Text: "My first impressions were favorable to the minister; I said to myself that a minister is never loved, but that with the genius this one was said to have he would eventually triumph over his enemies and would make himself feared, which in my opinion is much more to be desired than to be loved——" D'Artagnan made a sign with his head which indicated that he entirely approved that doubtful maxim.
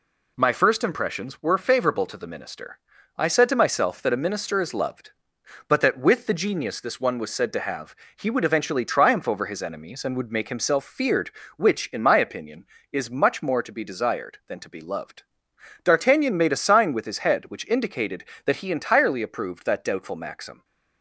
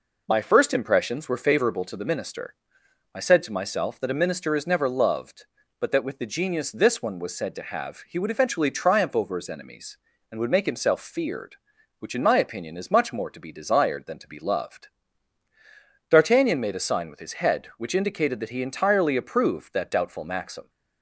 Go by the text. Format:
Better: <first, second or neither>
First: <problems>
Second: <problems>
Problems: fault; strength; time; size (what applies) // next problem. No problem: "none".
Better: second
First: skips "never"; at 4.7 s // pauses between "have" and "he"; slight; at 7.9 s; 0.22 s long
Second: none